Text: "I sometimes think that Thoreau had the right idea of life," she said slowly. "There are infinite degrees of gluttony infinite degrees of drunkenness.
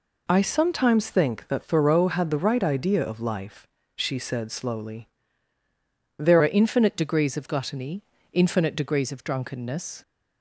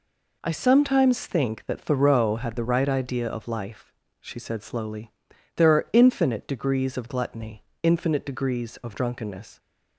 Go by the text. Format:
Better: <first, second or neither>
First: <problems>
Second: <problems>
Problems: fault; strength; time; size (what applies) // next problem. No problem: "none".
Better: second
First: changes voice at "are"; from 6.4 s on; 3.6 s long // pauses between "gluttony" and "infinite"; slight; at 8.0 s; 0.32 s long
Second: pauses between "gluttony" and "infinite"; slight; at 7.6 s; 0.18 s long